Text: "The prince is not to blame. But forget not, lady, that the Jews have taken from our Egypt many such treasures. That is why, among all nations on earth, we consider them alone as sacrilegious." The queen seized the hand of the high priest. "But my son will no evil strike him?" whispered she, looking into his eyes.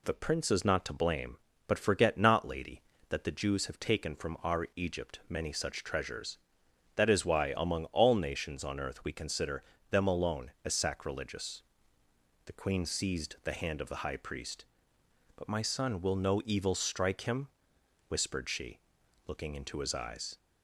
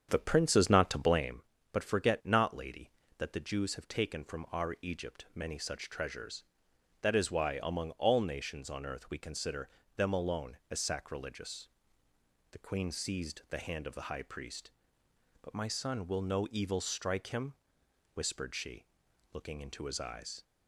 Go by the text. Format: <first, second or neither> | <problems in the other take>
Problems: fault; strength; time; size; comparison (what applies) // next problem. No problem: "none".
first | starts louder than the rest; strong; until 1.4 s; 8 dB // pauses between "consider" and "them"; slight; at 9.6 s; 0.26 s long; slight in the first